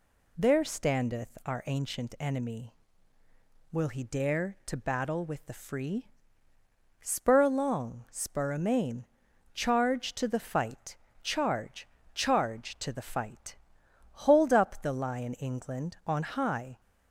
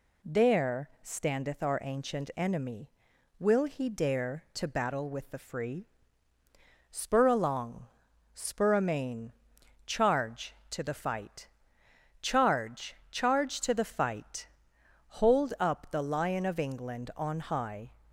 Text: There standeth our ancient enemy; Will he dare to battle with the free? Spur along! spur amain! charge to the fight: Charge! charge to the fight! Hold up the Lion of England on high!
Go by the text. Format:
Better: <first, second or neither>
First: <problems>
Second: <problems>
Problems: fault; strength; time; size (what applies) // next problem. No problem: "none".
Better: second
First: skips "of"; at 15.3 s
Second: none